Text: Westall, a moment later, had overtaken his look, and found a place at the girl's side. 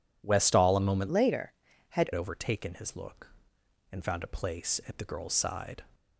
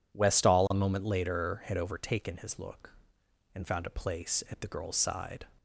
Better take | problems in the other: second | changes voice from "later" to "had"; from 1.1 to 2.1 s; 1.0 s long

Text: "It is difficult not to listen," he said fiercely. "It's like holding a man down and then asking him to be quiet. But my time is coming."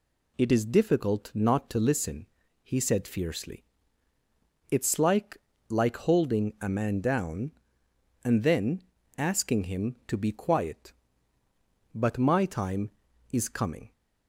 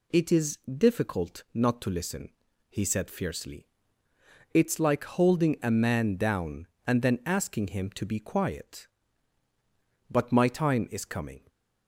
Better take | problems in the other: second | says "like" twice; at 5.6 s // pauses between "then" and "asking"; slight; at 8.8 s; 0.34 s long

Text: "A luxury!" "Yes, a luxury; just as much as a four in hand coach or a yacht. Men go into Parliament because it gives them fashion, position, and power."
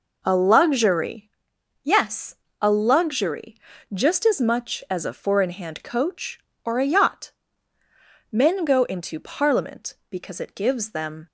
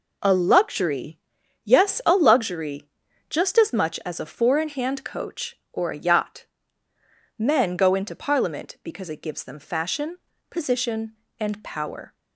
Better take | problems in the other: second | stops before "fashion position and power"; at 11.2 s

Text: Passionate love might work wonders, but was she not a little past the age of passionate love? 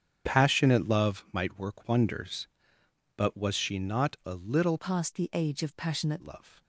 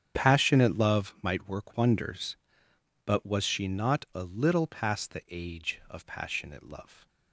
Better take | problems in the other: second | starts louder than the rest; strong; until 1.3 s; 8 dB; strong in the second // changes voice from "past" to "passionate"; from 4.7 to 6.2 s; 1.5 s long

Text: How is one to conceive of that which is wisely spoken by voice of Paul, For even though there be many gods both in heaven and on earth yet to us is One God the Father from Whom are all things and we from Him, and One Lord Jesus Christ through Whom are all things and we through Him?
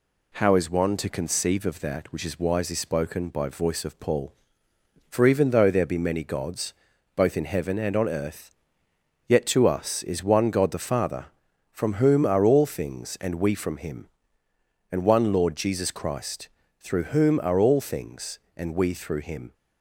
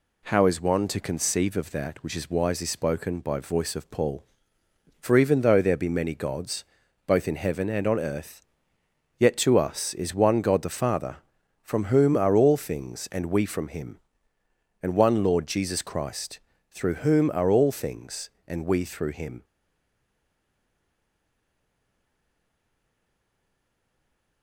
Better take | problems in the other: first | pauses between "gods" and "both"; at 6.6 s; 0.42 s long; also in the first // pauses between "earth" and "yet"; noticeable; at 8.3 s; 0.78 s long; noticeable in the first // pauses between "Christ" and "through"; slight; at 16.3 s; 0.32 s long; slight in the first // stays silent after the last word; strong; from 19.4 s on; 5.0 s long

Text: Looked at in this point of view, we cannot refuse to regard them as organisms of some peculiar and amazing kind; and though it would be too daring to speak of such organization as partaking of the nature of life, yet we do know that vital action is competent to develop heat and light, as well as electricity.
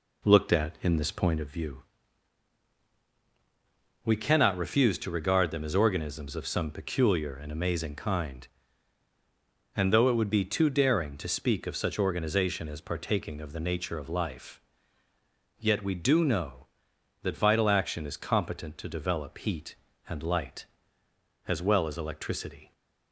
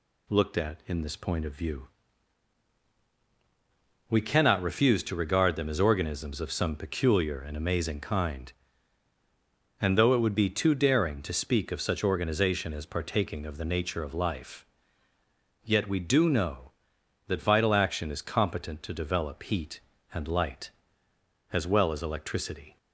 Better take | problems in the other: second | starts louder than the rest; slight; until 1.5 s; 3.5 dB

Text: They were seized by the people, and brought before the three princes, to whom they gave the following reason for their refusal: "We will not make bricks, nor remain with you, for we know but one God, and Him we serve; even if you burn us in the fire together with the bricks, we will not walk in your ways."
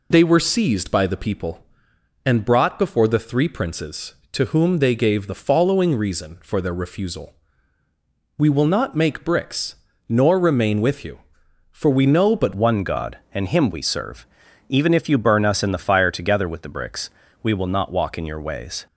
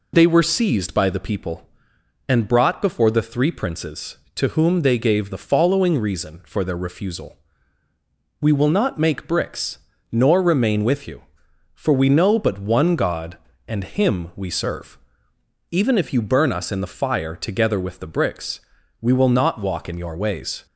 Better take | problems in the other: second | changes voice at "one"; from 12.5 s on; 6.3 s long

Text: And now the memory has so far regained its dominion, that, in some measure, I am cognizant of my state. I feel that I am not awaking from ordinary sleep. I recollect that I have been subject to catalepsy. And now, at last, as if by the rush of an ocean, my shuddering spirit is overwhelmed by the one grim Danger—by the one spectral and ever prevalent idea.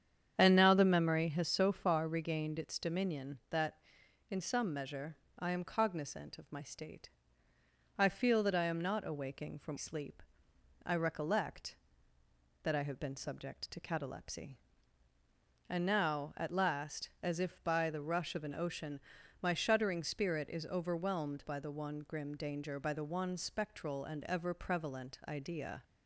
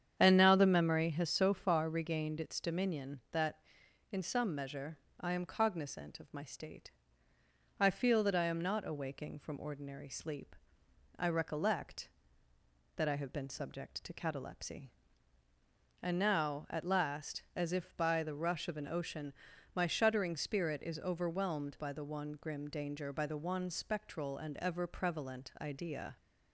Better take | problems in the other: second | starts louder than the rest; strong; until 1.3 s; 8.5 dB; strong in the second // skips "ordinary"; at 9.7 s

